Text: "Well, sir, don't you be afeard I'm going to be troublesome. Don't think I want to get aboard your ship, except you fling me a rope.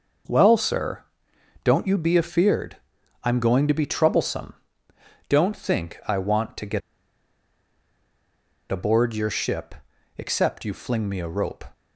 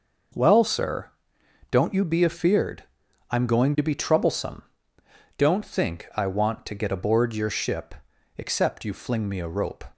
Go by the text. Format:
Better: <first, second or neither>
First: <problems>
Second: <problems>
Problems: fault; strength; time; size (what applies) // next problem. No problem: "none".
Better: second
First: pauses between "afeard" and "I'm"; at 2.7 s; 0.44 s long // pauses between "get" and "aboard"; strong; at 6.8 s; 1.9 s long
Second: pauses between "afeard" and "I'm"; at 2.8 s; 0.44 s long